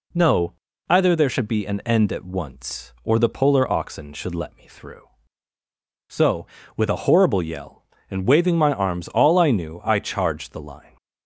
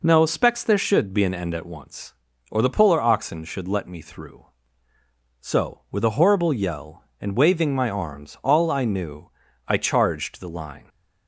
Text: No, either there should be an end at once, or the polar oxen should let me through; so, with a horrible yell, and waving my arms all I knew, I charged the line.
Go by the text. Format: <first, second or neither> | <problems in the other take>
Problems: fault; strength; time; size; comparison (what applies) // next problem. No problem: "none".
first | says "specs" for "either"; at 0.2 s